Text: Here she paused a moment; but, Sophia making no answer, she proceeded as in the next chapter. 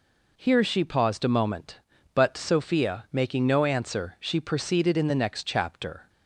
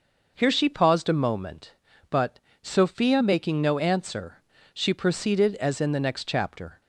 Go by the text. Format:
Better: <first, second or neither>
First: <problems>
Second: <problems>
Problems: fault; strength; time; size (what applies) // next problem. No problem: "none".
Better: second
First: skips "as"; at 4.9 s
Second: none